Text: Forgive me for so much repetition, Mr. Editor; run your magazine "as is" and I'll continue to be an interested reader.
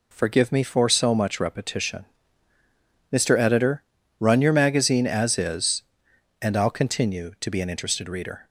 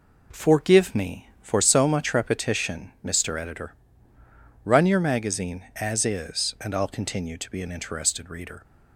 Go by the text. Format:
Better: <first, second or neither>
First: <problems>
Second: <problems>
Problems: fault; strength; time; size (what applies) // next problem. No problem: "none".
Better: neither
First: none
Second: none